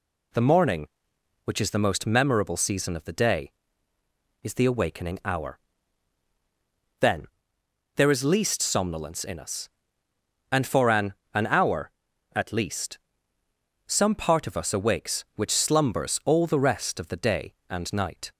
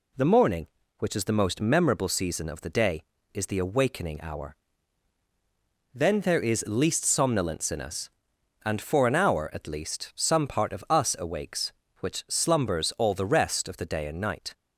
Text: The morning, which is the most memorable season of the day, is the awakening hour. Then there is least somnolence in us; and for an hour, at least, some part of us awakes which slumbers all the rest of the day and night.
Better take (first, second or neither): second